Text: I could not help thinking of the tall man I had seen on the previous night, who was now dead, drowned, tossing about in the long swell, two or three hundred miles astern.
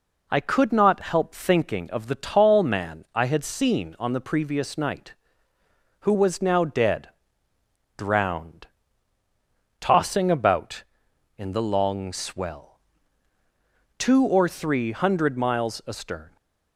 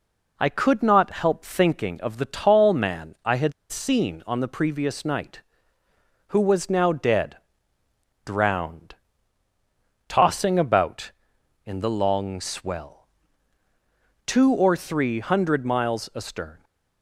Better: first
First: none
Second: pauses between "had" and "seen"; slight; at 3.5 s; 0.19 s long

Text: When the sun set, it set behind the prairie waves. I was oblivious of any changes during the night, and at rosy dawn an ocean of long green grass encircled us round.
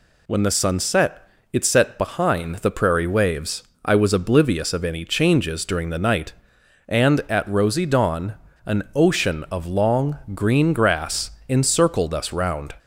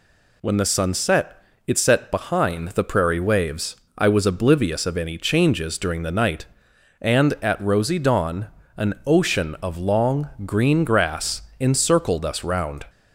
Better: neither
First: pauses between "dawn" and "an"; slight; at 8.3 s; 0.31 s long // pauses between "long" and "green"; slight; at 10.1 s; 0.16 s long // pauses between "grass" and "encircled"; slight; at 11.3 s; 0.16 s long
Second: pauses between "dawn" and "an"; slight; at 8.4 s; 0.30 s long // pauses between "long" and "green"; slight; at 10.2 s; 0.16 s long // pauses between "grass" and "encircled"; slight; at 11.4 s; 0.16 s long

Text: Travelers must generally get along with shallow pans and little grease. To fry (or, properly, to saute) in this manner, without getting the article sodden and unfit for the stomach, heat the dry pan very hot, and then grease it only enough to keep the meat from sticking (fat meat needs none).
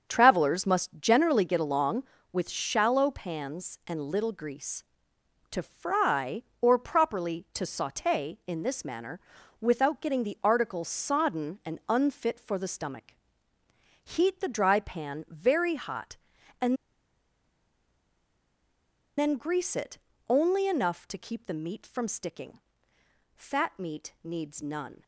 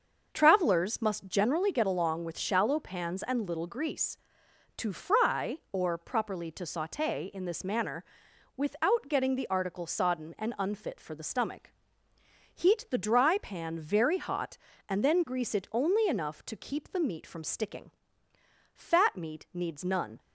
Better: second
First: starts louder than the rest; strong; until 1.1 s; 7 dB // pauses between "and" and "then"; strong; at 16.7 s; 2.4 s long // pauses between "it" and "only"; slight; at 19.9 s; 0.32 s long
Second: starts louder than the rest; until 1.3 s; 6 dB

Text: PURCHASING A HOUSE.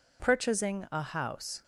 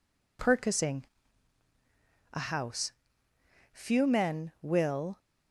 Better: first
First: none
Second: pauses between "PURCHASING" and "A"; strong; at 1.0 s; 1.2 s long // goes on to say "Few men will"; from 3.7 s on; 1.4 s long

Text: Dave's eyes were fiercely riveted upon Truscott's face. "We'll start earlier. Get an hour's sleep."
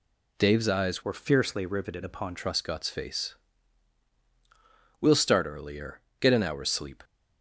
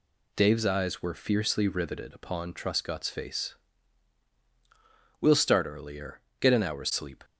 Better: second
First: changes voice from "were" to "upon"; from 1.0 to 2.3 s; 1.3 s long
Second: none

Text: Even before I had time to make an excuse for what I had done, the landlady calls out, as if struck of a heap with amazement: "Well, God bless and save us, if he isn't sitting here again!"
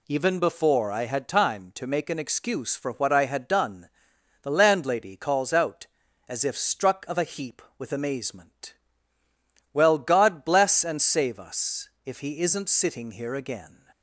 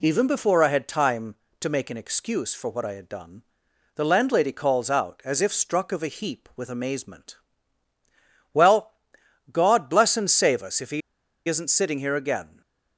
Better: first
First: none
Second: pauses between "he" and "isn't"; noticeable; at 11.0 s; 0.48 s long

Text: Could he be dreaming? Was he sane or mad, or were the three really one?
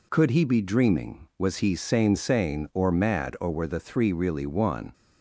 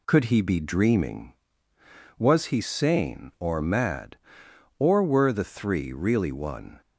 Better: second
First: says "sane" twice; at 2.1 s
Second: none

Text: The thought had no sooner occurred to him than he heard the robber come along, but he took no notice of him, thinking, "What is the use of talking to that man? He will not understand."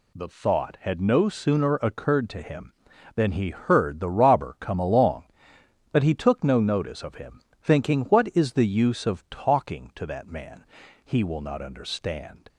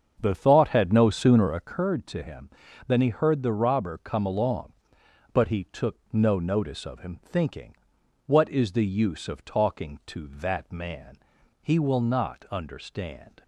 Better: first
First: none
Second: starts louder than the rest; until 1.8 s; 7 dB // pauses between "took" and "no"; slight; at 5.9 s; 0.16 s long

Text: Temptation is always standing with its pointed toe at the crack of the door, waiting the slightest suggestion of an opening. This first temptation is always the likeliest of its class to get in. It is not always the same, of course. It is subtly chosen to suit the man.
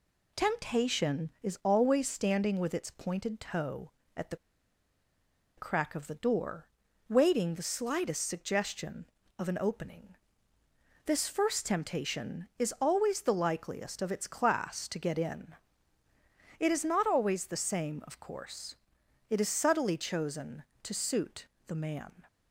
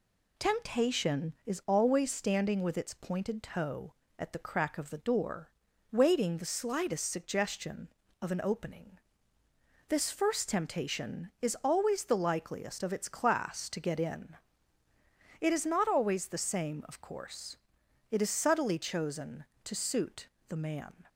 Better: second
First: pauses between "the" and "crack"; at 4.3 s; 1.2 s long // pauses between "suit" and "the"; slight; at 21.4 s; 0.20 s long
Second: pauses between "suit" and "the"; slight; at 20.2 s; 0.20 s long

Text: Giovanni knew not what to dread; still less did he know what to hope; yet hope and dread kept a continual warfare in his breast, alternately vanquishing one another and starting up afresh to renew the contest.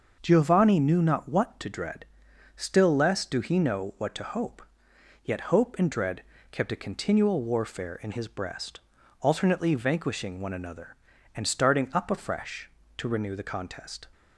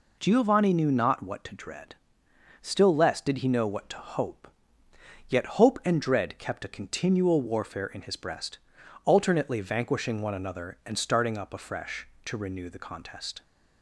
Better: second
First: starts louder than the rest; until 1.2 s; 6.5 dB // says "do" for "did"; at 3.2 s // pauses between "dread" and "kept"; slight; at 6.2 s; 0.28 s long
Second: none

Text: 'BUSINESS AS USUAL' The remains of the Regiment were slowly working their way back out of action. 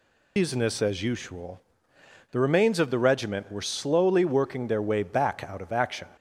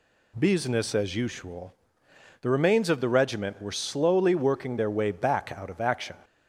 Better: second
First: loses the start of "BUSINESS"; at 0.3 s; 150 ms // pauses between "USUAL" and "The"; noticeable; at 1.5 s; 0.72 s long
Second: pauses between "USUAL" and "The"; noticeable; at 1.7 s; 0.68 s long

